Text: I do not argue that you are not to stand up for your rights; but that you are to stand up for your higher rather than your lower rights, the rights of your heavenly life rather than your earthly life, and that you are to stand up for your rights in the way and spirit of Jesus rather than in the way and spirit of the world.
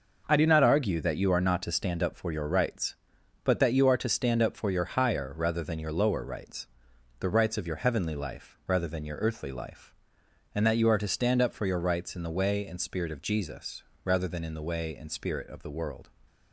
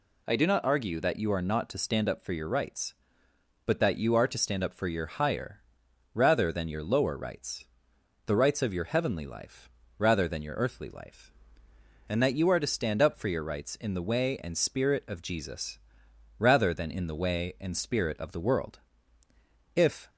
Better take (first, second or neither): first